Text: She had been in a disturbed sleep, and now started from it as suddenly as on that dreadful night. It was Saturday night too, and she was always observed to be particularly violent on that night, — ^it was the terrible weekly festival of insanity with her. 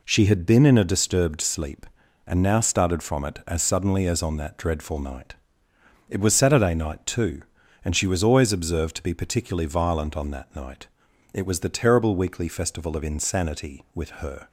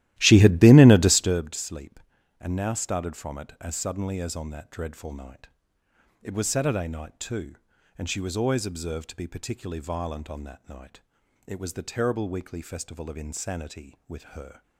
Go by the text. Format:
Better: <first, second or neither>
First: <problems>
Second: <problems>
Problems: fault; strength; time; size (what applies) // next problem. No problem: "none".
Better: first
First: none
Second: starts louder than the rest; strong; until 1.5 s; 15 dB